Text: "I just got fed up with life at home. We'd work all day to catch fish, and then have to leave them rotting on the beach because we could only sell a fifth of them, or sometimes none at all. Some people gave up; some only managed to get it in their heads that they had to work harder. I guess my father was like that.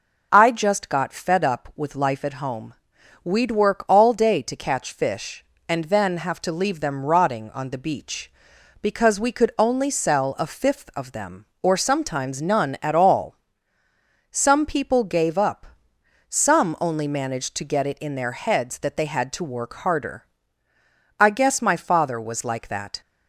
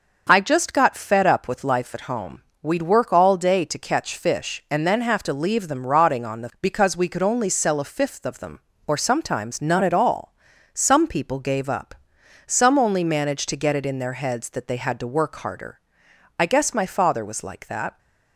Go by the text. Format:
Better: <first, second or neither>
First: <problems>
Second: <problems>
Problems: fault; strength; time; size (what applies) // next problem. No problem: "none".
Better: first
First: none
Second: skips "beach"; at 6.5 s